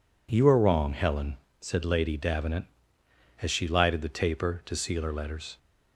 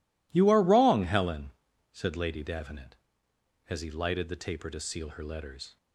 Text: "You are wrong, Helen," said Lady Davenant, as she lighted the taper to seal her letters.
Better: first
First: none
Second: says "he" for "she"; at 3.8 s

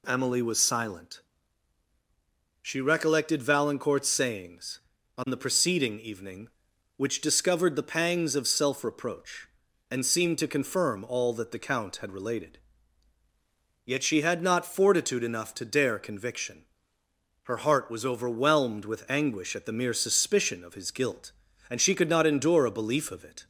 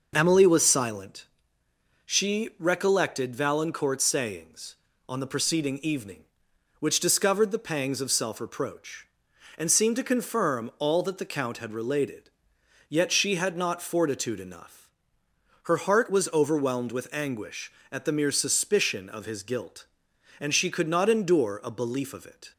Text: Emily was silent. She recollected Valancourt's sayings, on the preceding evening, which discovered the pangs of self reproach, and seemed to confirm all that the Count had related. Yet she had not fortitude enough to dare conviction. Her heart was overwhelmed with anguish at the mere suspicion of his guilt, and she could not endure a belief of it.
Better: first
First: none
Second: skips "to dare conviction"; at 15.2 s

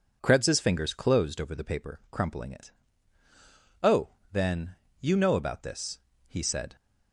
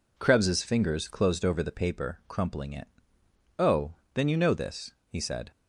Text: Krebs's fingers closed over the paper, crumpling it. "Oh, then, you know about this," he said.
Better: first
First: none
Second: skips "about"; at 4.5 s

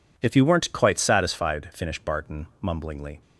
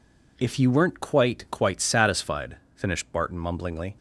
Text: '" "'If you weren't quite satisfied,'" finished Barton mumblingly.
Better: first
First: none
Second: says "quite" twice; at 1.5 s

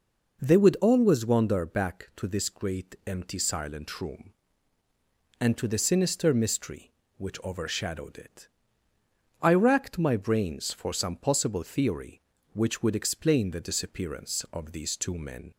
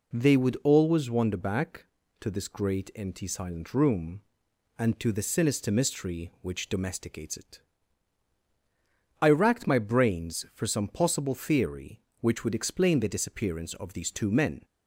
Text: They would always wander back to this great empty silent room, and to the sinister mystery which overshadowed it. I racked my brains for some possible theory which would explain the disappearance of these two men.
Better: first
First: none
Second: says "domesticates" for "overshadowed"; at 6.6 s

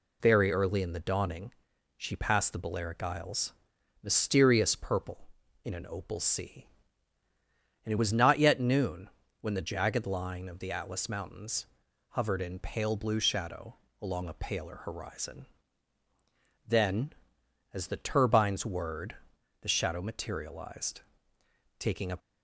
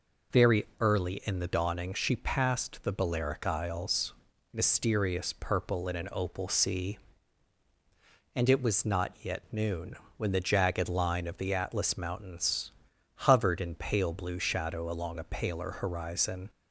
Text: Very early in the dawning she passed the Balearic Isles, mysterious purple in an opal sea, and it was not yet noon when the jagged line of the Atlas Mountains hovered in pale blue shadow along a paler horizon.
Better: second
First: pauses between "dawning" and "she"; at 1.5 s; 0.44 s long // pauses between "noon" and "when"; slight; at 9.0 s; 0.32 s long // pauses between "Mountains" and "hovered"; at 11.6 s; 0.44 s long // pauses between "shadow" and "along"; slight; at 13.7 s; 0.26 s long // goes on to say "Then as the turbines whirred the shadow materialized taking a"; strong; from 16.6 s on; 5.5 s long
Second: pauses between "noon" and "when"; slight; at 9.9 s; 0.22 s long // pauses between "Mountains" and "hovered"; noticeable; at 12.7 s; 0.46 s long

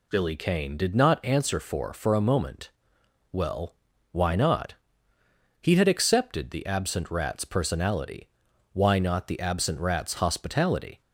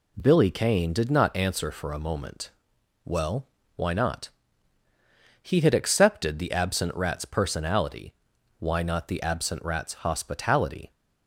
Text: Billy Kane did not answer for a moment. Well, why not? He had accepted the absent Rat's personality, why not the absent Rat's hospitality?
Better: second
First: says "for" twice; at 1.9 s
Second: none

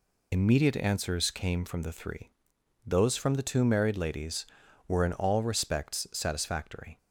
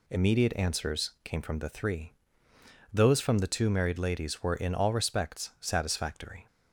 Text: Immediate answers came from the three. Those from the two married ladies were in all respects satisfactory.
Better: second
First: loses the start of "Immediate"; at 0.3 s; 65 ms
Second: none

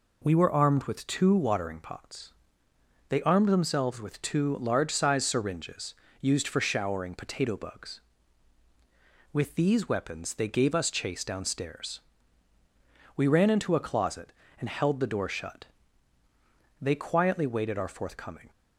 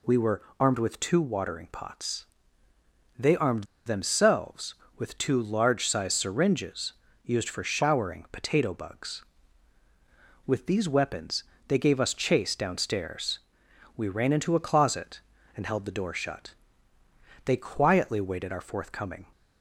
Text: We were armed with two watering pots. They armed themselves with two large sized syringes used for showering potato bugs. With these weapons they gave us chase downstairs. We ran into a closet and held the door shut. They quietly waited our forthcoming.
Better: first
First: pauses between "syringes" and "used"; slight; at 5.9 s; 0.26 s long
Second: pauses between "were" and "armed"; slight; at 0.4 s; 0.18 s long // pauses between "armed" and "themselves"; slight; at 3.6 s; 0.21 s long // pauses between "syringes" and "used"; slight; at 6.9 s; 0.32 s long // pauses between "weapons" and "they"; slight; at 11.4 s; 0.24 s long

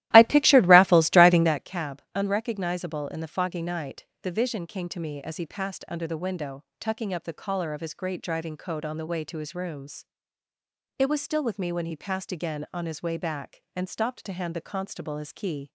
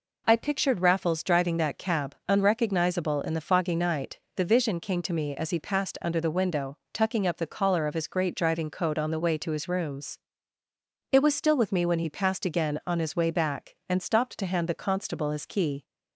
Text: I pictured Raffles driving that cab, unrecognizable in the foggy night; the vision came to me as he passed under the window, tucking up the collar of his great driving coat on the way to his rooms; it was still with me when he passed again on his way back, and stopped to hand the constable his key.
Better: second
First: starts louder than the rest; strong; until 1.6 s; 15 dB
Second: none

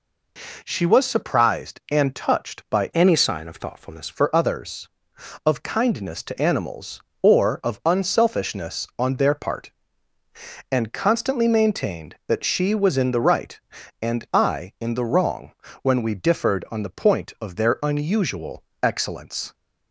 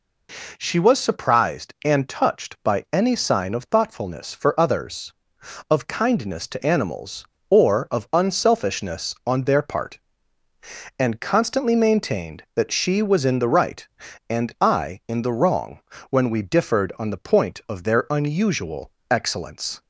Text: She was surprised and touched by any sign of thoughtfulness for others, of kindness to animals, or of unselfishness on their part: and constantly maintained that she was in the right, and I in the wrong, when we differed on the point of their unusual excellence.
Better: second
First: changes voice from "any" to "thoughtfulness"; from 2.9 to 4.0 s; 1.1 s long // pauses between "unusual" and "excellence"; slight; at 18.6 s; 0.22 s long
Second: pauses between "unusual" and "excellence"; slight; at 18.8 s; 0.22 s long

